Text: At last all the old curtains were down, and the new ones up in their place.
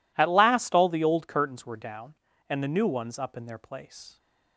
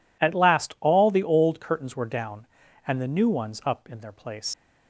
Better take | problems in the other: first | leaves "place" unfinished; at 4.5 s; 105 ms

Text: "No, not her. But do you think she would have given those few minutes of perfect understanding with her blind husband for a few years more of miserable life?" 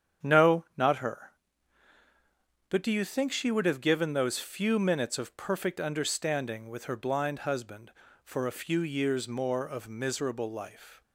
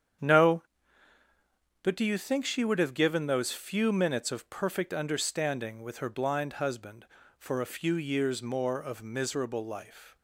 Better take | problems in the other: first | starts louder than the rest; strong; until 2.4 s; 8.5 dB; strong in the first // skips "not her"; at 1.2 s

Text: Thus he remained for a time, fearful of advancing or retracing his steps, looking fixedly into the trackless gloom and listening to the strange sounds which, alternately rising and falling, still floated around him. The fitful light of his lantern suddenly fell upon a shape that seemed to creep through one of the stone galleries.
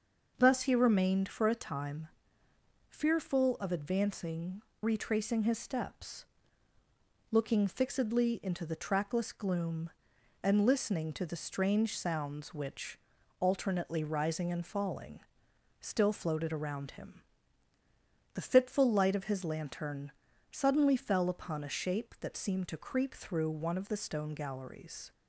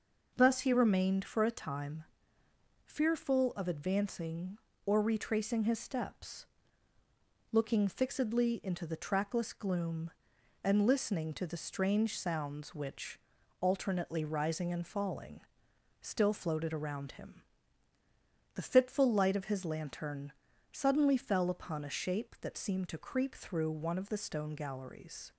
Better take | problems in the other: second | skips "or"; at 4.7 s // pauses between "lantern" and "suddenly"; at 20.1 s; 0.40 s long; also in the second

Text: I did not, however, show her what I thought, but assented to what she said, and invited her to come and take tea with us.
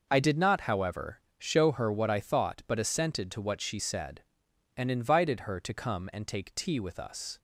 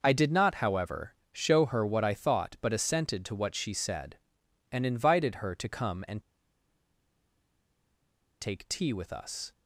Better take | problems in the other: first | pauses between "and" and "take"; strong; at 6.2 s; 2.2 s long

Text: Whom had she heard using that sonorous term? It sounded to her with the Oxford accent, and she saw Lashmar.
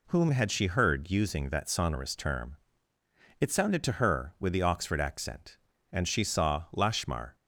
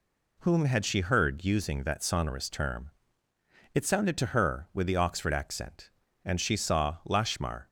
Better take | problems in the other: neither | none

